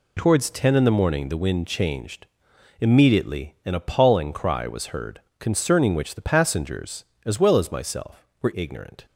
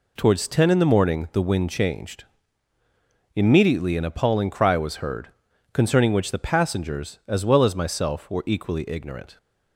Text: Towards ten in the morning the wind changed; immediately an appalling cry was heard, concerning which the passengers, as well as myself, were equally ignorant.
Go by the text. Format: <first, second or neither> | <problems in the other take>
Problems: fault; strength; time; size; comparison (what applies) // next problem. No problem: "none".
second | skips "equally"; at 8.5 s